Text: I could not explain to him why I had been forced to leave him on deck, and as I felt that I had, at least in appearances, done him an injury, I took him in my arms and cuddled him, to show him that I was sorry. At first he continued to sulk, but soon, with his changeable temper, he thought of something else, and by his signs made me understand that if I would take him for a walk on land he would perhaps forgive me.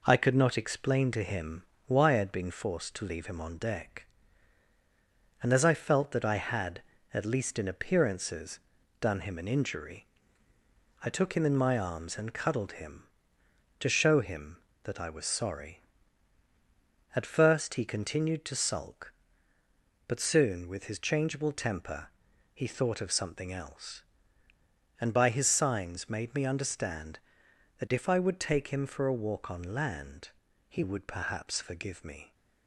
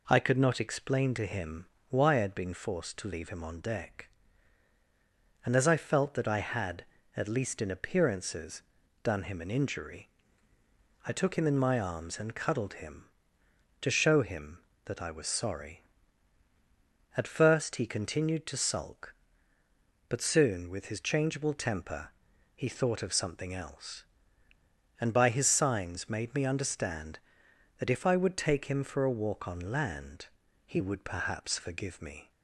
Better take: second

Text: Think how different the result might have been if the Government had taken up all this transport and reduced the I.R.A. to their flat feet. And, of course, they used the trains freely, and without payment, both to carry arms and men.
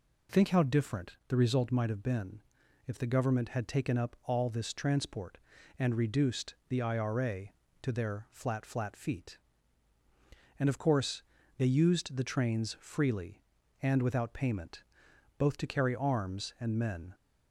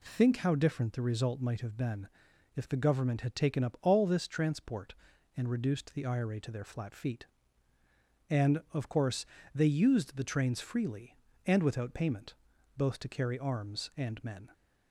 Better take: second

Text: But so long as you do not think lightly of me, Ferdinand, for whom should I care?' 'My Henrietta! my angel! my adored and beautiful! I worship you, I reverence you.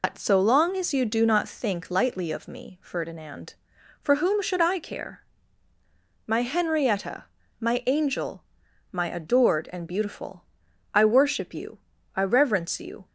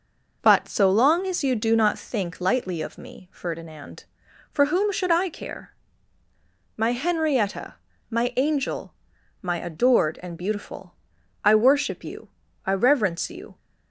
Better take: second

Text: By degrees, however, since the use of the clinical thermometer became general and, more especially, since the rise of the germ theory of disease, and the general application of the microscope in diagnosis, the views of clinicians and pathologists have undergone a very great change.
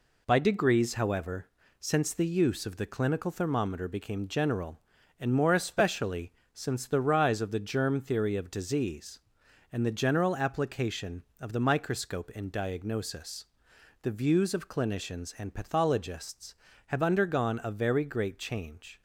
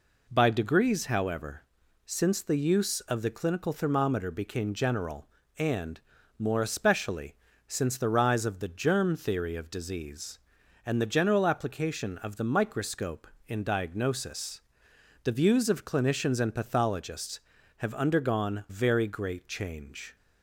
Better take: first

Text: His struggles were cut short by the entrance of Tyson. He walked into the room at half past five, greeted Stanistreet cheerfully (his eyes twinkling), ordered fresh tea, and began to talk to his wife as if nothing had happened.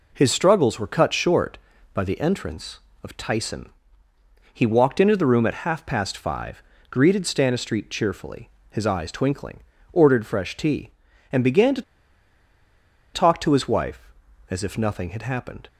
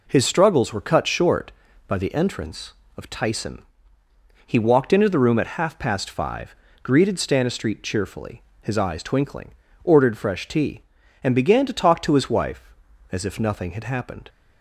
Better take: second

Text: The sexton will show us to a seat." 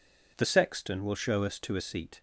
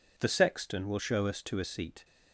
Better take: neither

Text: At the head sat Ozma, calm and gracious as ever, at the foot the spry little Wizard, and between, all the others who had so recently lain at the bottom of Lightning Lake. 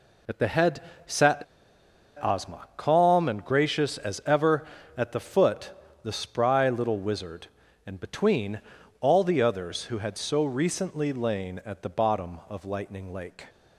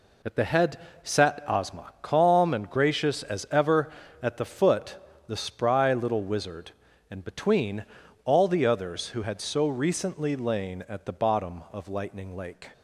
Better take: second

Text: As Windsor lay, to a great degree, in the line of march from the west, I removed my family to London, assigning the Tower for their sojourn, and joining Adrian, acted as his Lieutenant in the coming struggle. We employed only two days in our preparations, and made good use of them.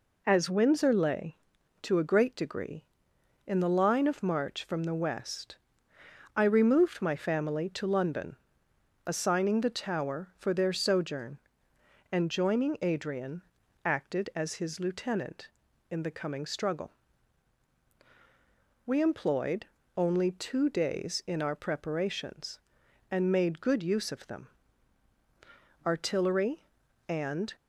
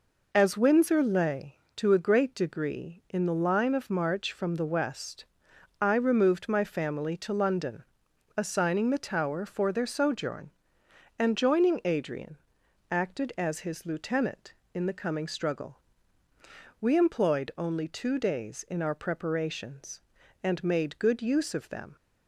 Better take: second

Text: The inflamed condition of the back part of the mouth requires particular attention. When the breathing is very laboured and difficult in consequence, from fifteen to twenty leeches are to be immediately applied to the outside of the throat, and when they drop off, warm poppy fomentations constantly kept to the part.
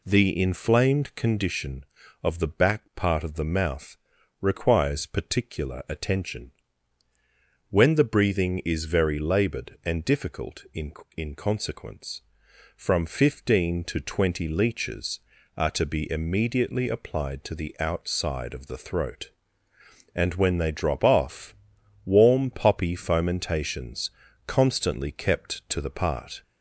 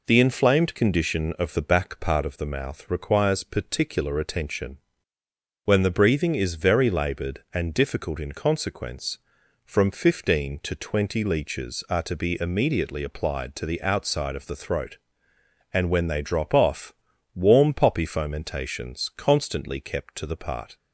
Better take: second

